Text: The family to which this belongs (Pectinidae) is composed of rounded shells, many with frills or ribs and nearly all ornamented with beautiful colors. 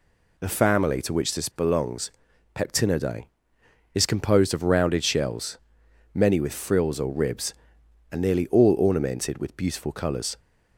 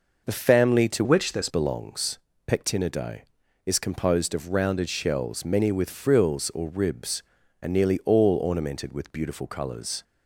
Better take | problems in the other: first | changes voice from "which" to "this"; from 1.0 to 1.4 s; 0.4 s long

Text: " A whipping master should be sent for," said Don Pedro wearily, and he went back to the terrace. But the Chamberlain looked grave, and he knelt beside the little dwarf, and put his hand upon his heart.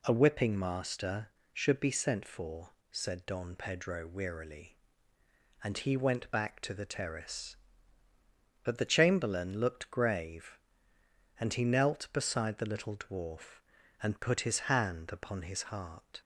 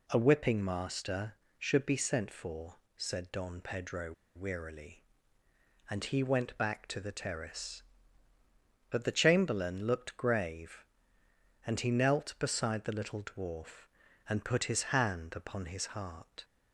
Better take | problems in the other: first | pauses between "Pedro" and "wearily"; slight; at 4.1 s; 0.22 s long

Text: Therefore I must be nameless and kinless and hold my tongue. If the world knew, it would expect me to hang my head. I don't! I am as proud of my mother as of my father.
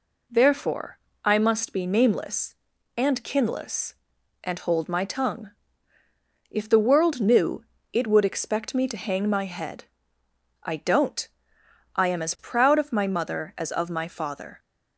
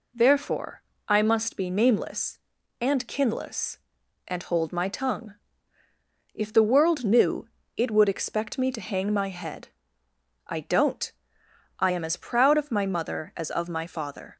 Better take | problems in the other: neither | pauses between "Therefore" and "I"; slight; the same in both

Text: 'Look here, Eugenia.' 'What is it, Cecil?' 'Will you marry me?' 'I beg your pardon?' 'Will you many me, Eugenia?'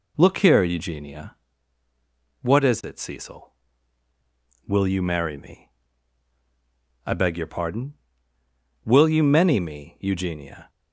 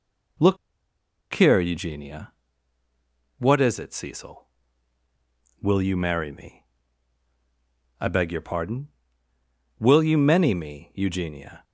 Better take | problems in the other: first | pauses between "Look" and "here"; noticeable; at 0.5 s; 0.78 s long

